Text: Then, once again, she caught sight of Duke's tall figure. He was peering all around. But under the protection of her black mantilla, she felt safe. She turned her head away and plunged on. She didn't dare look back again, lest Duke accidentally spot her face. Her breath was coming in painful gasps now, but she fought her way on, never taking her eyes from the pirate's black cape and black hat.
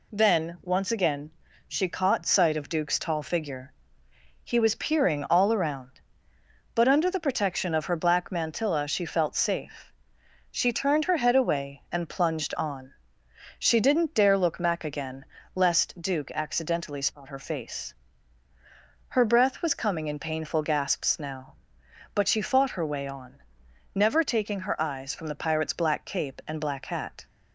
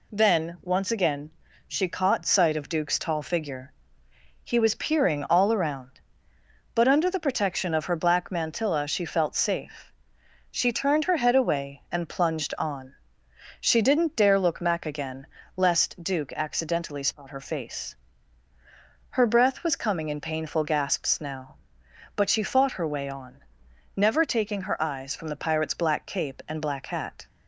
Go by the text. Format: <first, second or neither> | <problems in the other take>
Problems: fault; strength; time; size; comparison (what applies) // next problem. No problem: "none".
neither | none